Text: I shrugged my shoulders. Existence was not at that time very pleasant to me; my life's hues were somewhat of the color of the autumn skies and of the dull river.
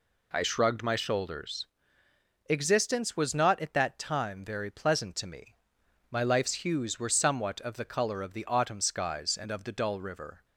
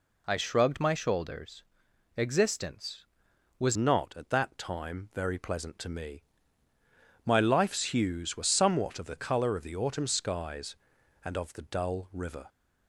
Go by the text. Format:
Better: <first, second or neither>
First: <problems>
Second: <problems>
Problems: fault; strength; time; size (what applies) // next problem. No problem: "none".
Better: first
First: none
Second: changes voice at "not"; from 3.7 s on; 8.7 s long